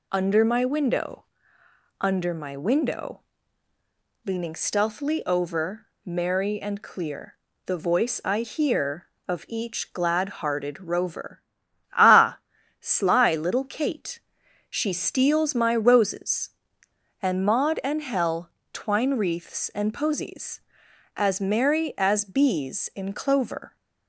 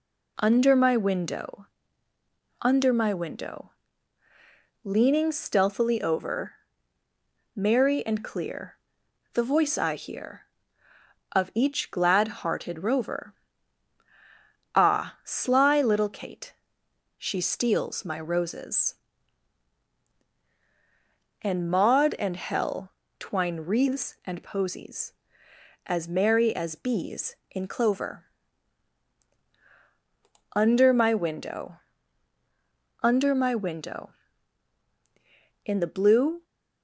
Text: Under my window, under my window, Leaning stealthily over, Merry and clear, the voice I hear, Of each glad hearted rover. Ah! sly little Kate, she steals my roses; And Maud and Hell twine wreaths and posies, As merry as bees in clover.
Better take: first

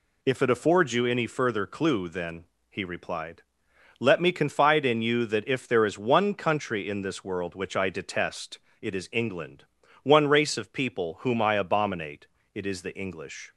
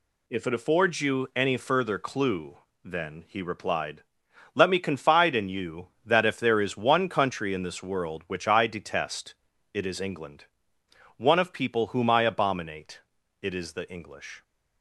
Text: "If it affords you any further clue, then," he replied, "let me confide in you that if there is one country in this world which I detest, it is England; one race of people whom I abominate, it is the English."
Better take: first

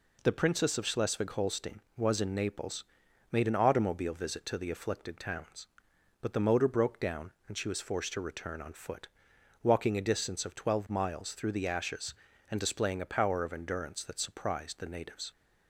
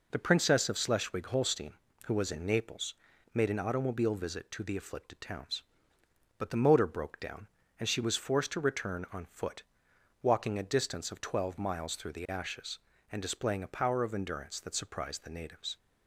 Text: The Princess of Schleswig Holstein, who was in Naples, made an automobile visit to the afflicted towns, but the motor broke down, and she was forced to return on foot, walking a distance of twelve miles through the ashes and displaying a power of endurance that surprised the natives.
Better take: second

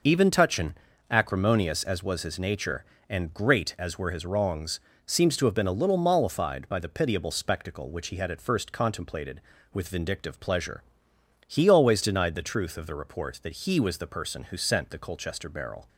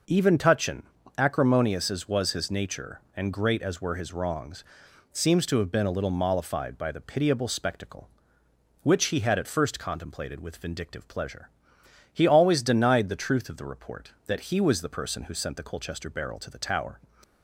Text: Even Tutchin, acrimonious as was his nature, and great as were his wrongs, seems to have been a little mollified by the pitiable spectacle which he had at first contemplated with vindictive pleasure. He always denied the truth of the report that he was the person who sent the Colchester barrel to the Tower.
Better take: second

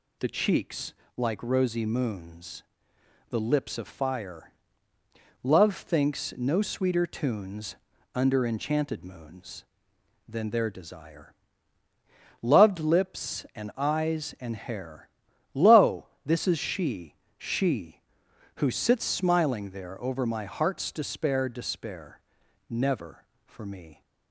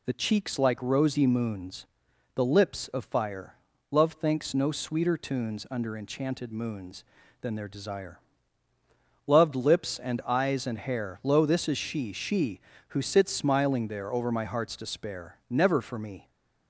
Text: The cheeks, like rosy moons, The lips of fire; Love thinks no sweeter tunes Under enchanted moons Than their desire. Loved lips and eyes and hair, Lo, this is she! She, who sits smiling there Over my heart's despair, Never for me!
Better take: second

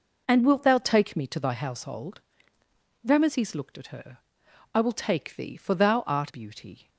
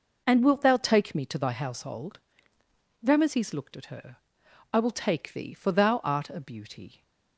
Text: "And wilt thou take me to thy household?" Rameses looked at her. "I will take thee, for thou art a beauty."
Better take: second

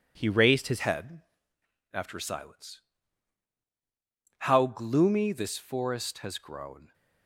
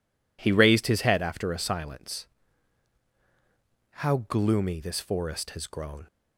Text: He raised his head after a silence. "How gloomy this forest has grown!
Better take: second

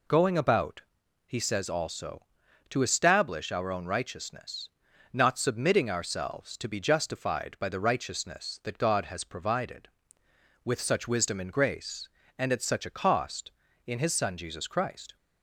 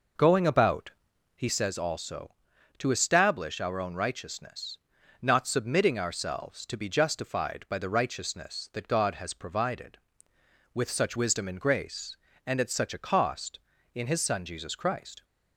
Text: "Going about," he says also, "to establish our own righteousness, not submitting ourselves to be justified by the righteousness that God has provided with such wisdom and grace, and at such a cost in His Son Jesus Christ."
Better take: first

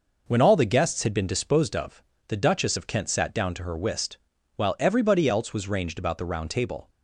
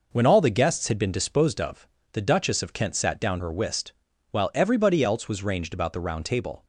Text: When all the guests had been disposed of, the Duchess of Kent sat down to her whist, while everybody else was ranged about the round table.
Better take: first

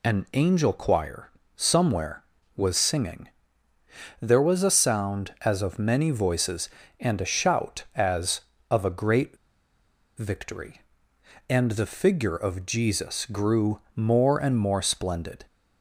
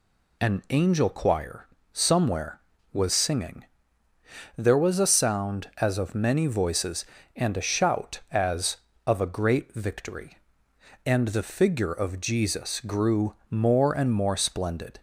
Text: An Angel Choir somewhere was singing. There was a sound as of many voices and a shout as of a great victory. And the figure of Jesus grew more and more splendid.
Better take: second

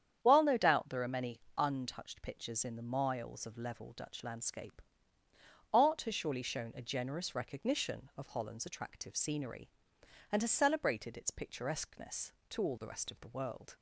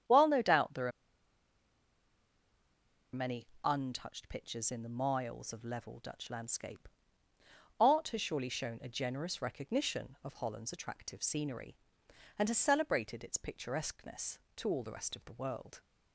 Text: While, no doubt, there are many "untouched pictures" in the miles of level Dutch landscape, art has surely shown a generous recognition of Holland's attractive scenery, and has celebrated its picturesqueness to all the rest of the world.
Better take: first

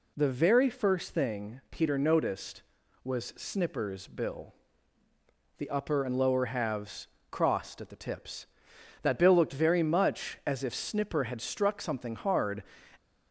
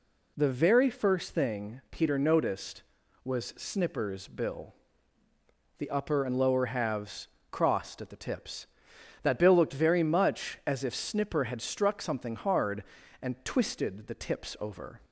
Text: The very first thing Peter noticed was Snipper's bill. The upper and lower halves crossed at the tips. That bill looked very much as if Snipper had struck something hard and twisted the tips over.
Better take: second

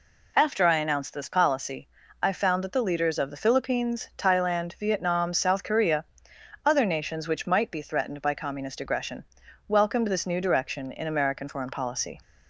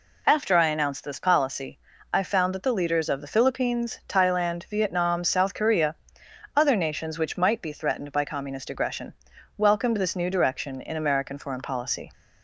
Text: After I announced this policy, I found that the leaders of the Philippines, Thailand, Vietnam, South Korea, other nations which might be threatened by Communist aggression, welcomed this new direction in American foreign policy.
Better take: neither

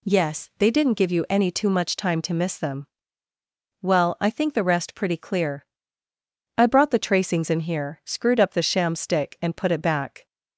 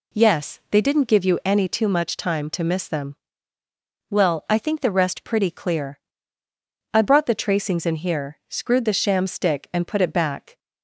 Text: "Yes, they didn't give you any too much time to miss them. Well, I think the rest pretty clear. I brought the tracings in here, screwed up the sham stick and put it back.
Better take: first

